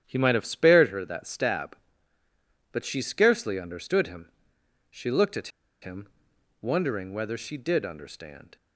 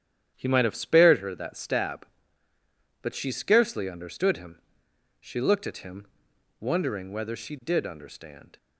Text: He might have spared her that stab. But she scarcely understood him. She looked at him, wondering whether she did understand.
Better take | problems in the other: second | starts louder than the rest; strong; until 1.0 s; 10 dB; strong in the second // pauses between "at" and "him"; slight; at 5.4 s; 0.33 s long

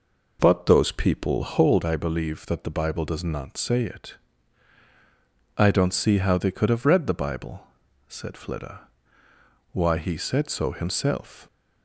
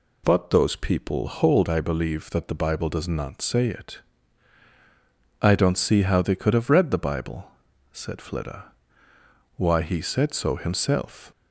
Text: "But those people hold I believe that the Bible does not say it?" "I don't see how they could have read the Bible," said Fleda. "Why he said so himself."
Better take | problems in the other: second | starts louder than the rest; noticeable; until 1.8 s; 5 dB

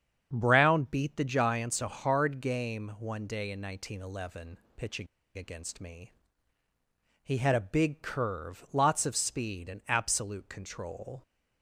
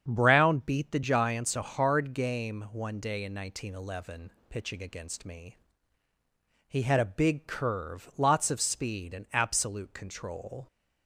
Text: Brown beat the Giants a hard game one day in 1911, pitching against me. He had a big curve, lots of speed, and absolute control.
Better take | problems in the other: second | starts louder than the rest; strong; until 1.3 s; 7 dB; strong in the second // pauses between "pitching" and "against"; slight; at 5.0 s; 0.31 s long

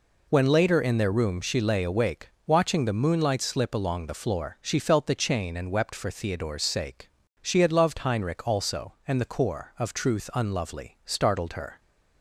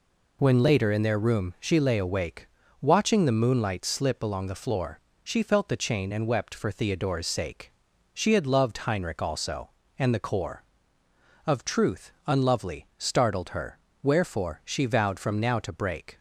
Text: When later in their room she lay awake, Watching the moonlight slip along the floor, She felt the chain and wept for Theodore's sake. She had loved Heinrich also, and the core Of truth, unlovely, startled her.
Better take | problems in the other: first | goes on to say "Wherefore She vowed from now to break"; strong; from 14.0 s on; 2.1 s long

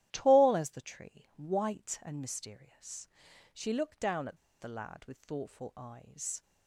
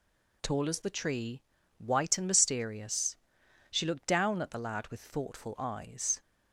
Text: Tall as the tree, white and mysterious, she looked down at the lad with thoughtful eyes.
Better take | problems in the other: second | starts louder than the rest; strong; until 1.1 s; 12.5 dB // pauses between "at" and "the"; slight; at 4.3 s; 0.24 s long

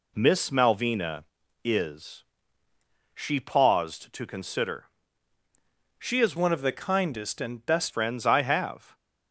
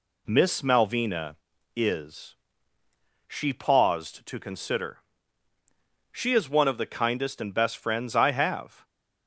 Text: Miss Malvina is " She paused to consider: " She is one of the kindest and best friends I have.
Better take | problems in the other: second | changes voice from "one" to "best"; from 6.3 to 7.9 s; 1.6 s long

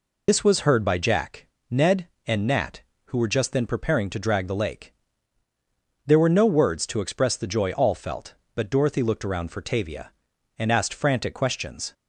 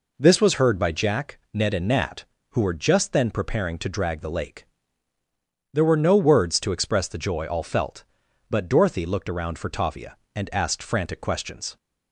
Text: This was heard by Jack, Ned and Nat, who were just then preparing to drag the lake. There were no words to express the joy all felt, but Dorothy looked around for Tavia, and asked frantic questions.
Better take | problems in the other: second | loses the start of "This"; at 0.2 s; 90 ms

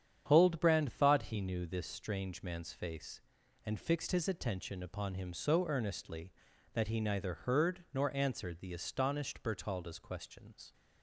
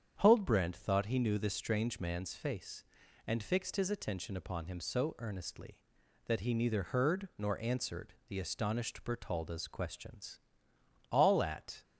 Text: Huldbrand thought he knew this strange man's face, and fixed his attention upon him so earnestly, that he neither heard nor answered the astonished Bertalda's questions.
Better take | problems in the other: first | starts louder than the rest; strong; until 1.2 s; 8 dB; strong in the first // goes on to say "All at"; noticeable; from 11.1 s on; 0.72 s long

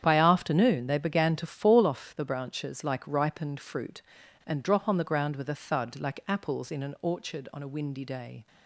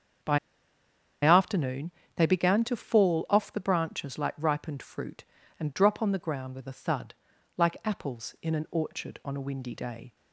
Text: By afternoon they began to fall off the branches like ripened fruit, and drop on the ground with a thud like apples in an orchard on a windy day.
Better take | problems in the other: first | starts louder than the rest; strong; until 2.3 s; 7.5 dB; strong in the first // pauses between "By" and "afternoon"; noticeable; at 0.3 s; 0.86 s long // pauses between "afternoon" and "they"; slight; at 1.9 s; 0.24 s long // pauses between "thud" and "like"; at 7.1 s; 0.44 s long

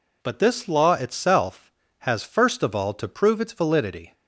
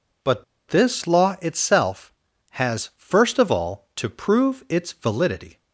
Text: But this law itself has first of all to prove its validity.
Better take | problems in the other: first | pauses between "But" and "this"; slight; at 0.4 s; 0.24 s long

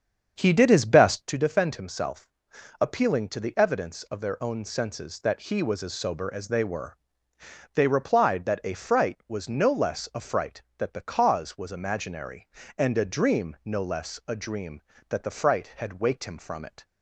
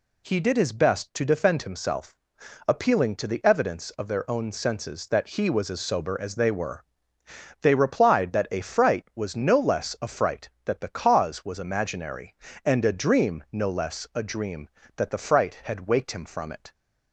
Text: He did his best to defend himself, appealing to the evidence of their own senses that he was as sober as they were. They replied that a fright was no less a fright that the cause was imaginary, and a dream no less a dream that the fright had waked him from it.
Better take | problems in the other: second | starts louder than the rest; strong; until 1.3 s; 7 dB

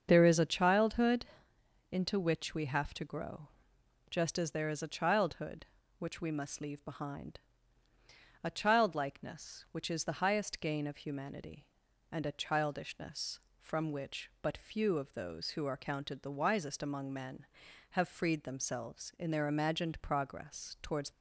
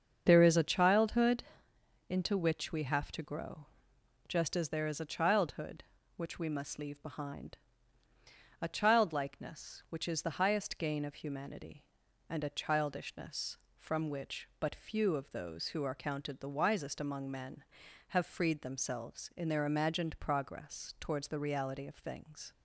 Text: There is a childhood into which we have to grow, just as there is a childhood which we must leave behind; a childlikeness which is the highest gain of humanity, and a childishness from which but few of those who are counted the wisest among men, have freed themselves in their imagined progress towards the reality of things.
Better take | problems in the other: second | starts louder than the rest; until 1.1 s; 7 dB; also in the second // pauses between "childhood" and "into"; noticeable; at 1.2 s; 0.66 s long; noticeable in the second // stops before "the reality of things"; at 21.1 s

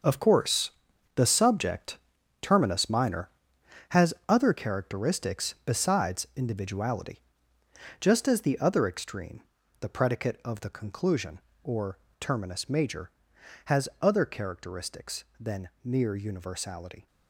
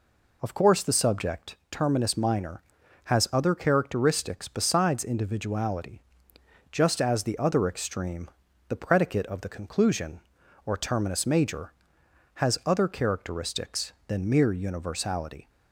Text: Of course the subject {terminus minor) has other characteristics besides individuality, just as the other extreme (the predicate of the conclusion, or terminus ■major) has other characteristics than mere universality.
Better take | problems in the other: second | gets quieter; strong; throughout; 11.5 dB // pauses between "course" and "the"; at 0.7 s; 0.44 s long // pauses between "or" and "terminus"; slight; at 11.9 s; 0.20 s long // pauses between "than" and "mere"; slight; at 15.6 s; 0.16 s long

